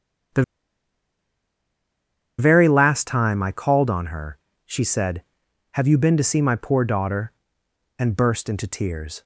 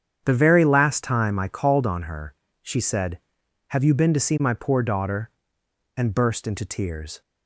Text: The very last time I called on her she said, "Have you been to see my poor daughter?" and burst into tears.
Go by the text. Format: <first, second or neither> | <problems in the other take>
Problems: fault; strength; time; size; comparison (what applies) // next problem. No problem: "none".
second | starts louder than the rest; strong; until 3.3 s; 8.5 dB; strong in the second // pauses between "The" and "very"; strong; at 0.4 s; 1.9 s long // pauses between "her" and "she"; slight; at 4.3 s; 0.28 s long; slight in the second